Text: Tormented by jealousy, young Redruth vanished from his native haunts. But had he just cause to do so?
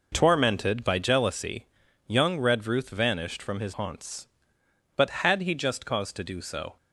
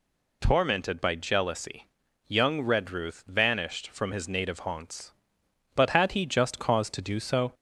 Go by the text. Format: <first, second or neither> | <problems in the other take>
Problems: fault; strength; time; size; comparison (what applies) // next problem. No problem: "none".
second | skips "native"; at 3.7 s